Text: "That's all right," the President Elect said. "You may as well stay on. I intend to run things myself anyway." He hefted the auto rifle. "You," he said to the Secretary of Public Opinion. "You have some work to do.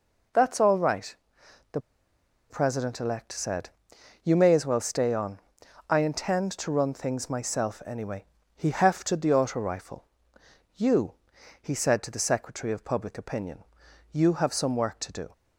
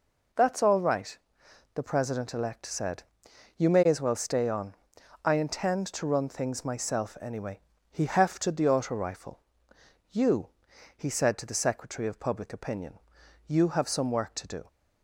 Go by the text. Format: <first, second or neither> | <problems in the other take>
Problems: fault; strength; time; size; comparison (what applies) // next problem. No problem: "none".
second | pauses between "the" and "President"; noticeable; at 1.7 s; 0.70 s long